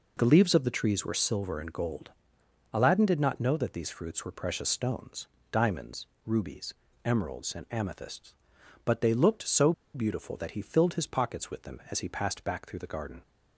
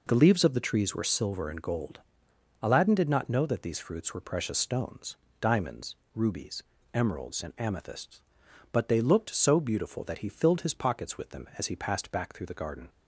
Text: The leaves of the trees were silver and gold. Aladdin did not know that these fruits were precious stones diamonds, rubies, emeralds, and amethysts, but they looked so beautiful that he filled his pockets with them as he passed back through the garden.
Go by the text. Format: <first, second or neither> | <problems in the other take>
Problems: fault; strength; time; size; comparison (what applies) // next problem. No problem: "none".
second | pauses between "stones" and "diamonds"; slight; at 5.2 s; 0.24 s long; slight in the second // pauses between "so" and "beautiful"; slight; at 9.7 s; 0.22 s long